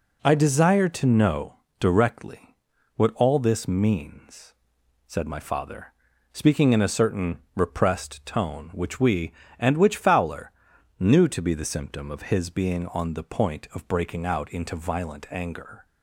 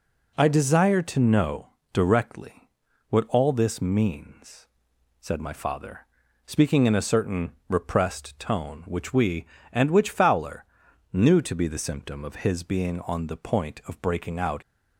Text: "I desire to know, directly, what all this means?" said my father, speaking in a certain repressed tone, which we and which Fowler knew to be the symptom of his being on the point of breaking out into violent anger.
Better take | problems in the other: first | pauses between "certain" and "repressed"; slight; at 7.5 s; 0.18 s long; slight in the first // pauses between "Fowler" and "knew"; noticeable; at 10.6 s; 0.48 s long; noticeable in the first // stops before "into violent anger"; at 14.6 s

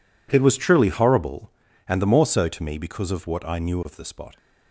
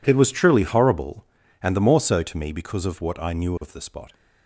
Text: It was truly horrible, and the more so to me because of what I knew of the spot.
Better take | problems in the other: neither | none

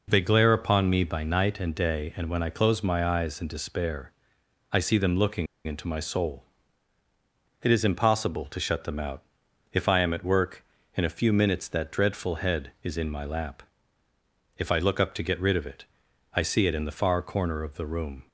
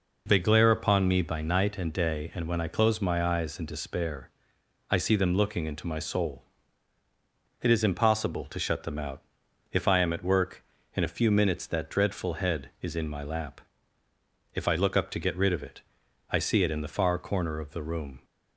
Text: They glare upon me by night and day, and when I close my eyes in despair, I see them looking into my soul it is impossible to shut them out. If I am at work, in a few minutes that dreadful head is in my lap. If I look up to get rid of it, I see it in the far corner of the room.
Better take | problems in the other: second | pauses between "looking" and "into"; slight; at 5.4 s; 0.19 s long // pauses between "soul" and "it"; at 6.4 s; 1.2 s long; also in the second

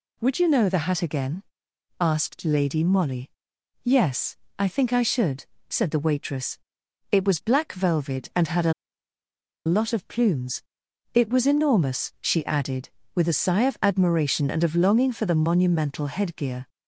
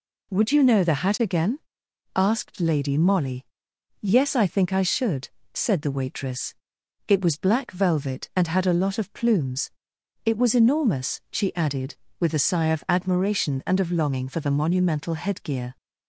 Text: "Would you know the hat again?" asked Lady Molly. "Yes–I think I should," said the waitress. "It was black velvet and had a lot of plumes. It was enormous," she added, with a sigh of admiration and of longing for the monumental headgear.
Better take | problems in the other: second | pauses between "a" and "lot"; noticeable; at 8.7 s; 0.93 s long

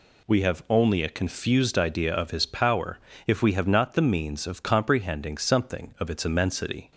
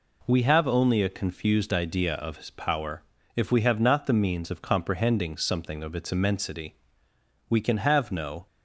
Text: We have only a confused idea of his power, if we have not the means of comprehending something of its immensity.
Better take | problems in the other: first | goes on to say "We can have no"; noticeable; from 7.4 s on; 0.98 s long

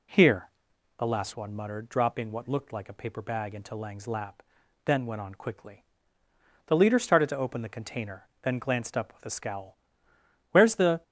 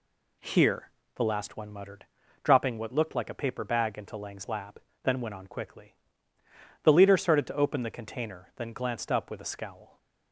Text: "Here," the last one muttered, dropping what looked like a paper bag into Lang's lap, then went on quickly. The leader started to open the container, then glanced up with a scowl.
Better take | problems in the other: second | goes on to say "Where's the"; from 10.5 s on; 0.52 s long

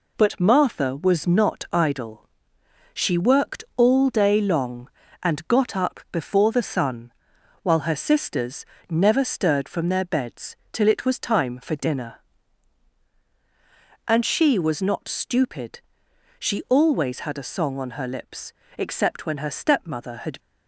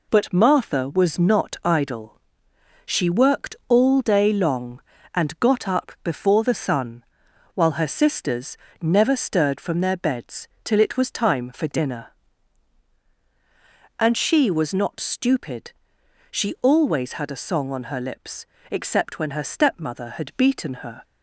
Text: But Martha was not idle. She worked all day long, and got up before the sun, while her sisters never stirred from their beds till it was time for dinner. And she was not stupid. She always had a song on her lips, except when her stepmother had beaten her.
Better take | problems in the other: second | pauses between "sisters" and "never"; slight; at 8.6 s; 0.26 s long; slight in the second // pauses between "beds" and "till"; slight; at 10.5 s; 0.16 s long; slight in the second // stops before "beaten her"; at 20.3 s

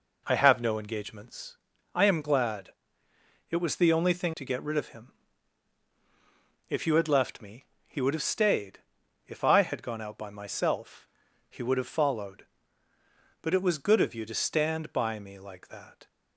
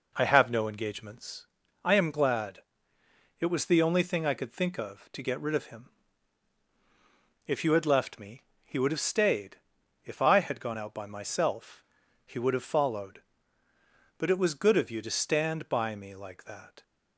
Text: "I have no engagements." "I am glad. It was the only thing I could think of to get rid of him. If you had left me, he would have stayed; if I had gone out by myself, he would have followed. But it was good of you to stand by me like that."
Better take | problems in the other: second | skips "I could think of"; at 4.3 s

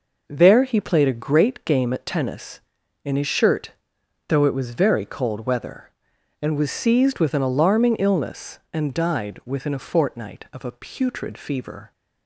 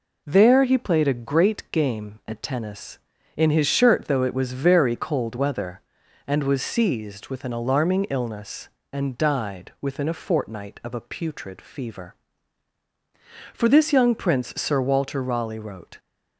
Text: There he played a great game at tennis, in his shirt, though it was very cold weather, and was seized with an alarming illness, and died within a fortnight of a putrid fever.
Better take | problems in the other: first | goes on to say "For this young prince Sir Walter Raleigh wrote"; strong; from 13.5 s on; 2.4 s long

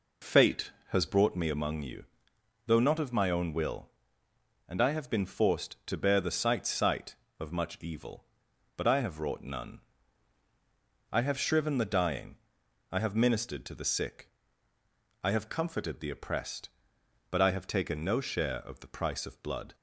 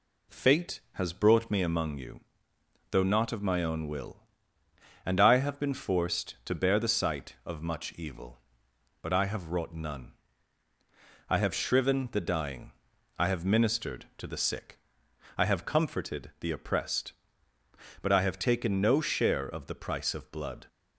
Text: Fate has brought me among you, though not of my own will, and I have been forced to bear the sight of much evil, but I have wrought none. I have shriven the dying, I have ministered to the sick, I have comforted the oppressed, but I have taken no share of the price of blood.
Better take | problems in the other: second | says "sight" twice; at 6.6 s

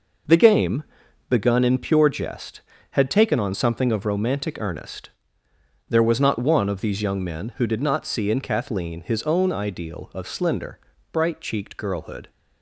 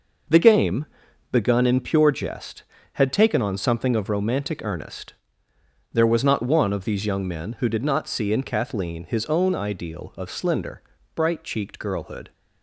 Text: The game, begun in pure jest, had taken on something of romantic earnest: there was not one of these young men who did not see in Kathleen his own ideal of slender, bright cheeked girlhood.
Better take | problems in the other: neither | none

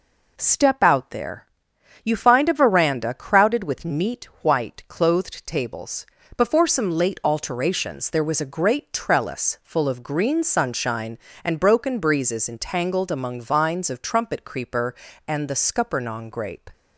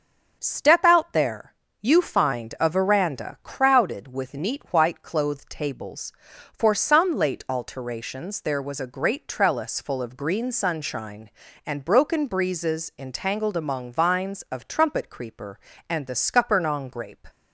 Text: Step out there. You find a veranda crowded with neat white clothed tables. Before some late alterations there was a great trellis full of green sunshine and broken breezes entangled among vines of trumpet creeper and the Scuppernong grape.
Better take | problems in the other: first | starts louder than the rest; until 1.4 s; 7 dB // says "For" for "Before"; at 6.5 s

